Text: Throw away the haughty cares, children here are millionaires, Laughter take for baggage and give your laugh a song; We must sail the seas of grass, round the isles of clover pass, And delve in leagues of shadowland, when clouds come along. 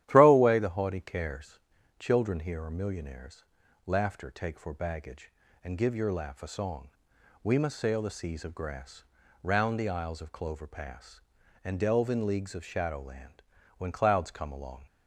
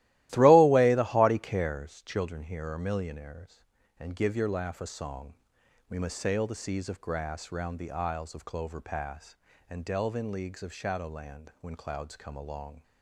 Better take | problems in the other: first | starts louder than the rest; strong; until 1.3 s; 15.5 dB; strong in the first // skips "Laughter take for baggage"; at 3.8 s

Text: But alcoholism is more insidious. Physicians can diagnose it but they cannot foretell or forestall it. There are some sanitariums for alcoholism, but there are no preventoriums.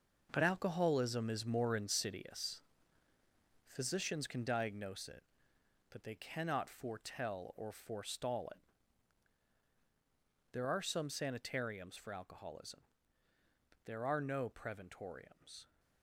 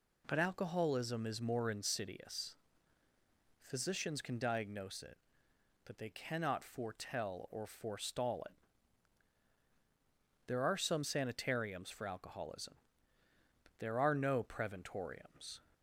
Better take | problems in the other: second | gets quieter; strong; throughout; 11 dB

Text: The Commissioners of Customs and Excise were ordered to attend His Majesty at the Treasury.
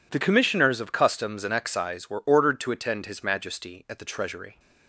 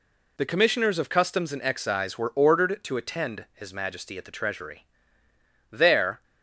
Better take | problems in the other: first | goes on to say "There"; from 5.7 s on; 0.52 s long

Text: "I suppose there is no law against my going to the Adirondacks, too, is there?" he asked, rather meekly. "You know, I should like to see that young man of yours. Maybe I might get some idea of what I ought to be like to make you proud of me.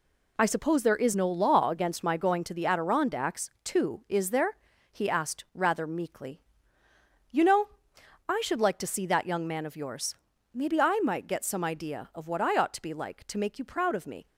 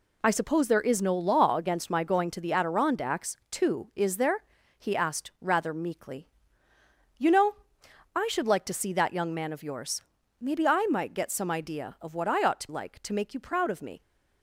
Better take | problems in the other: first | skips "be"; at 12.6 s

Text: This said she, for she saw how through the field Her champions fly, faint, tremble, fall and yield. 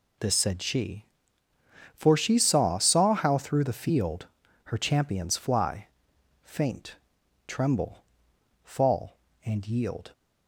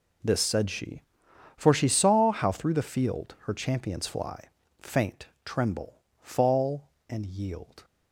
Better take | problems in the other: second | says "saw" twice; at 2.7 s // pauses between "field" and "Her"; at 4.2 s; 0.38 s long

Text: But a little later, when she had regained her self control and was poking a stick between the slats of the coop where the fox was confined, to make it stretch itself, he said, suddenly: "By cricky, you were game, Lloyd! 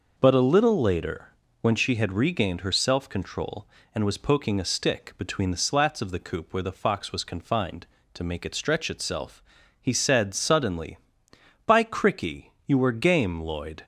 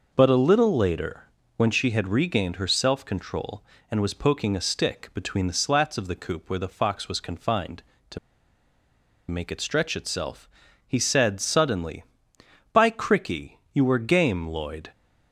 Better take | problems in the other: first | pauses between "to" and "make"; at 8.1 s; 1.1 s long

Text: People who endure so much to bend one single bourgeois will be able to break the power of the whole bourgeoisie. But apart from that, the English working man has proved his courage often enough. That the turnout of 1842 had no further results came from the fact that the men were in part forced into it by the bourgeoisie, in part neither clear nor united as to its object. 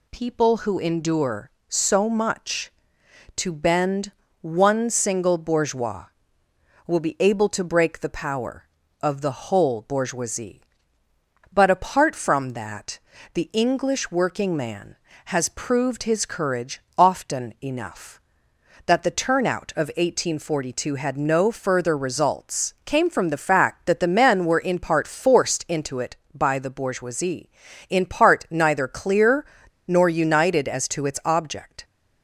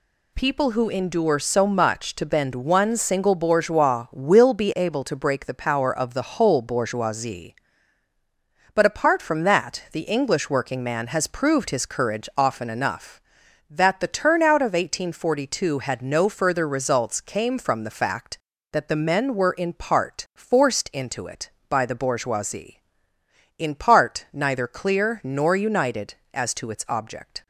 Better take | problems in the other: second | pauses between "bend" and "one"; slight; at 4.1 s; 0.28 s long // pauses between "courage" and "often"; slight; at 16.7 s; 0.18 s long // pauses between "clear" and "nor"; at 29.4 s; 0.42 s long

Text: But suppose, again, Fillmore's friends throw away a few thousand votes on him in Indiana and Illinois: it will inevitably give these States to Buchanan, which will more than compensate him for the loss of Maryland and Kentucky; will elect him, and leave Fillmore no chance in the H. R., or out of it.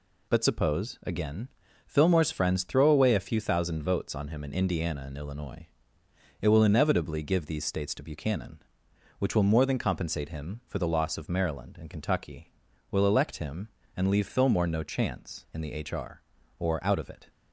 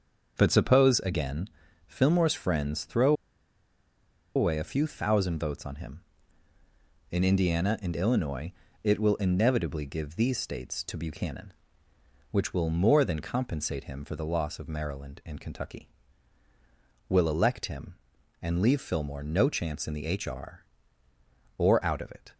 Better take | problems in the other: first | starts louder than the rest; until 1.3 s; 6.5 dB // pauses between "throw" and "away"; at 3.1 s; 1.2 s long

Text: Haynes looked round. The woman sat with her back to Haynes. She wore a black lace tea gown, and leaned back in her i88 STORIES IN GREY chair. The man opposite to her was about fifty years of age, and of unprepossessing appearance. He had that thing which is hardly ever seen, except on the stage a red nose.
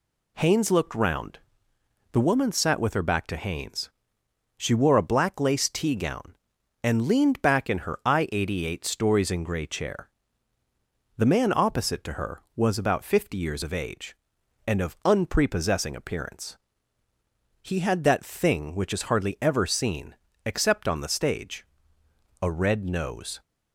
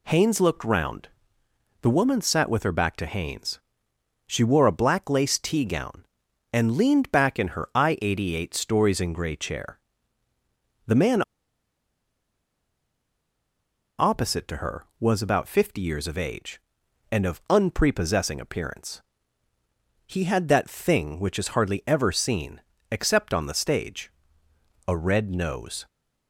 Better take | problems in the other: first | pauses between "man" and "opposite"; strong; at 11.2 s; 2.7 s long // pauses between "stage" and "a"; noticeable; at 24.1 s; 0.76 s long; noticeable in the first

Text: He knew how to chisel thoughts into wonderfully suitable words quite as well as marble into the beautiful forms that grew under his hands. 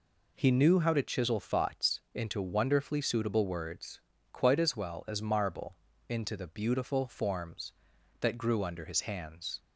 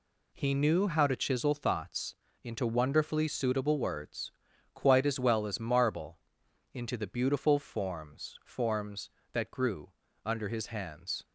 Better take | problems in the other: first | pauses between "thoughts" and "into"; slight; at 2.1 s; 0.28 s long // pauses between "words" and "quite"; at 4.3 s; 0.42 s long; slight in the first // pauses between "marble" and "into"; noticeable; at 6.1 s; 0.54 s long; slight in the first // says "forms" twice; at 8.4 s // pauses between "grew" and "under"; slight; at 9.9 s; 0.32 s long

